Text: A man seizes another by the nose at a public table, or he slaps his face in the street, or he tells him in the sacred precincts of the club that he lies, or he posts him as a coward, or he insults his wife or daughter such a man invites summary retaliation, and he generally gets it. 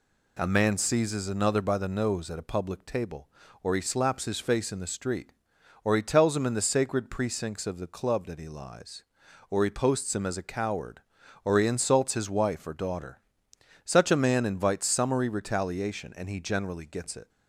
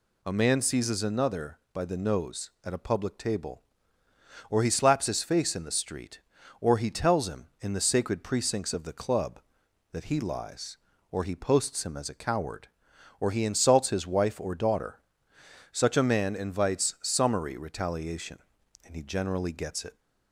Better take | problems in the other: neither | pauses between "daughter" and "such"; noticeable; the same in both

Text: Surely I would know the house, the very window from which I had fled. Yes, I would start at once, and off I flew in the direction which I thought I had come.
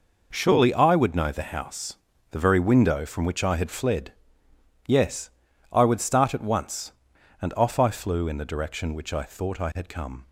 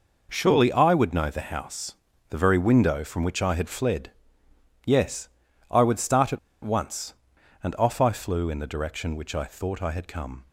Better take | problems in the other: first | pauses between "at" and "once"; slight; at 6.3 s; 0.24 s long

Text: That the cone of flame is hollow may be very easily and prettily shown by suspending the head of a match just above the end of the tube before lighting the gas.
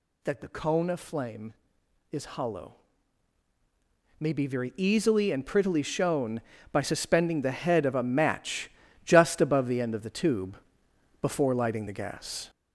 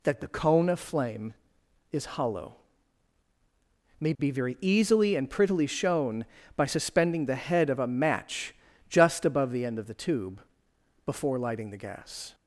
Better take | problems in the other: second | gets louder; noticeable; throughout; 4.5 dB // pauses between "hollow" and "may"; strong; at 2.7 s; 1.4 s long; strong in the second // pauses between "match" and "just"; slight; at 8.6 s; 0.36 s long; slight in the second // pauses between "tube" and "before"; noticeable; at 10.5 s; 0.64 s long; noticeable in the second

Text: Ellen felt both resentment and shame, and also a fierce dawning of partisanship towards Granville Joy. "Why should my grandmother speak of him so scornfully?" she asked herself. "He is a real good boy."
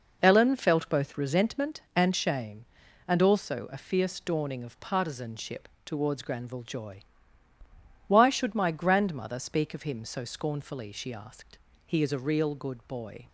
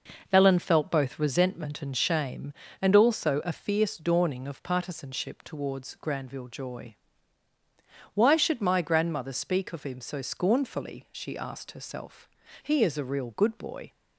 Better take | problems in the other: second | pauses between "partisanship" and "towards"; slight; at 5.6 s; 0.18 s long // skips "herself"; at 11.7 s

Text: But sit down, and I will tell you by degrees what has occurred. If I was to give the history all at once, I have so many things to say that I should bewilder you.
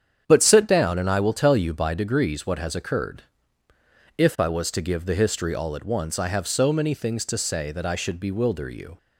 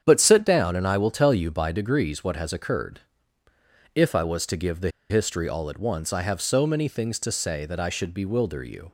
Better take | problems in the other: first | starts louder than the rest; strong; until 1.0 s; 8 dB; strong in the first // pauses between "the" and "history"; slight; at 4.9 s; 0.19 s long

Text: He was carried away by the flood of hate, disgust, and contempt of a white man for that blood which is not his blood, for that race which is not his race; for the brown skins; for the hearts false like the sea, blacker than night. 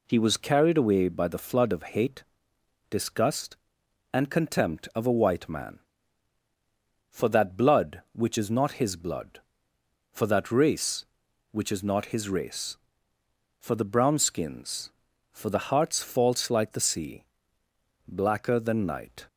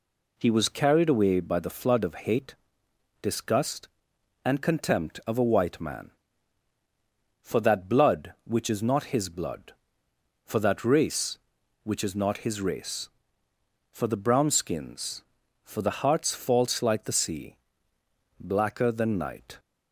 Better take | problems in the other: neither | none

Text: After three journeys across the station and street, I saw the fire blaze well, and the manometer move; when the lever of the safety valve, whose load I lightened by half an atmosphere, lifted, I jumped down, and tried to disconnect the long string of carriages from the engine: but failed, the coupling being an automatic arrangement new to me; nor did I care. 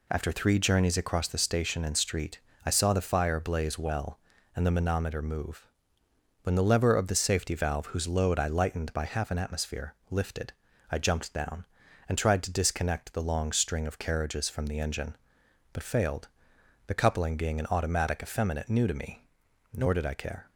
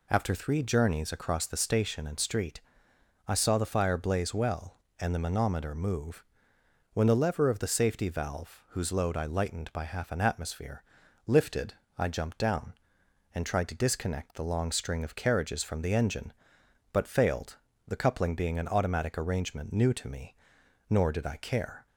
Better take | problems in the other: second | says "effeminate" for "arrangement"; at 18.2 s

